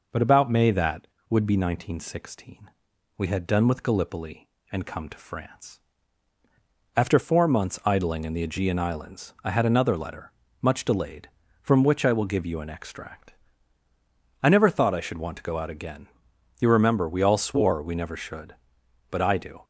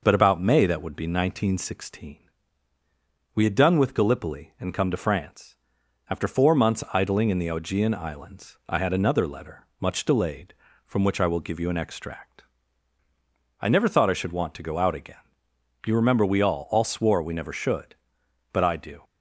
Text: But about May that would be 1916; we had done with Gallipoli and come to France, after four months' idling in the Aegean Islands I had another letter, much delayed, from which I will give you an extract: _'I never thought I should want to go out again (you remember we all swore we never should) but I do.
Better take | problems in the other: first | says "all" twice; at 16.6 s

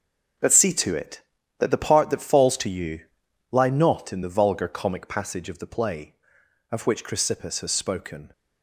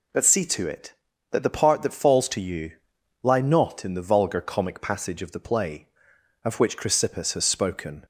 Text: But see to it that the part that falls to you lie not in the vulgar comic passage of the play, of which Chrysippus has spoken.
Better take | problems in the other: second | gets quieter; strong; throughout; 10.5 dB // pauses between "you" and "lie"; noticeable; at 3.0 s; 0.50 s long; noticeable in the second

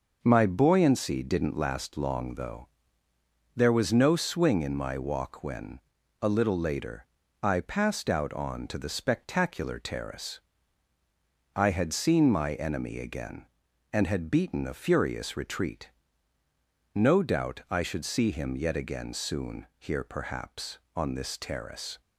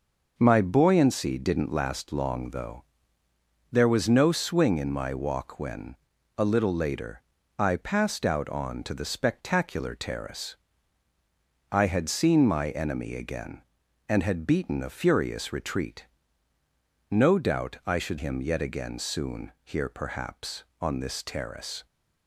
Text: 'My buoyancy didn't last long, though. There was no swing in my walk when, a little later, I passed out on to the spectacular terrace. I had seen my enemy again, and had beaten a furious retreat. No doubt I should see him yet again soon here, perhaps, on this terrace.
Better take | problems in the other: first | skips "see"; at 18.1 s

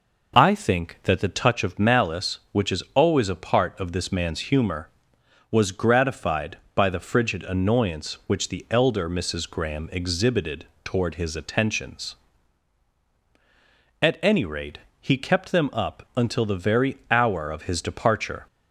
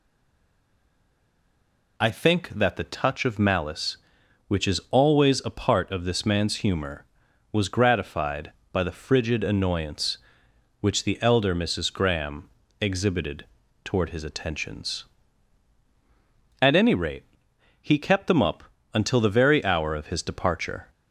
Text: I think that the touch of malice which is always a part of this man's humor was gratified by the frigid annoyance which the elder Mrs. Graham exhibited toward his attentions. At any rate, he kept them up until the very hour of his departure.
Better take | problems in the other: first | stays silent before the first word; noticeable; until 1.9 s; 1.9 s long // pauses between "Graham" and "exhibited"; slight; at 12.4 s; 0.32 s long // pauses between "exhibited" and "toward"; slight; at 13.4 s; 0.36 s long; slight in the first // pauses between "up" and "until"; slight; at 18.6 s; 0.32 s long

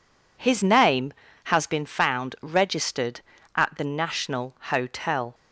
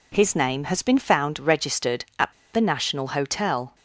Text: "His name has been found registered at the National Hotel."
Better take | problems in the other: first | pauses between "at" and "the"; slight; at 2.3 s; 0.20 s long

